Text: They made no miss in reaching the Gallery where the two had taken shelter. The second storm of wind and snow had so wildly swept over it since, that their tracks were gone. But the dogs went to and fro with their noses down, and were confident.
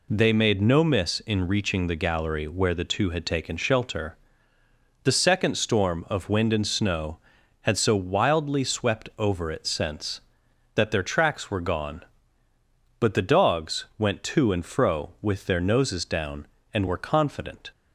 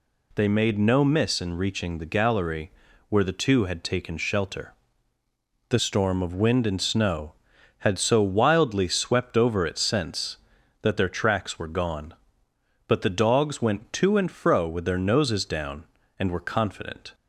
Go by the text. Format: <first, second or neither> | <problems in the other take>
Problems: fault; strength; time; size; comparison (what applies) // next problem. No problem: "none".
first | pauses between "Gallery" and "where"; at 2.7 s; 0.38 s long // skips "second"; at 5.7 s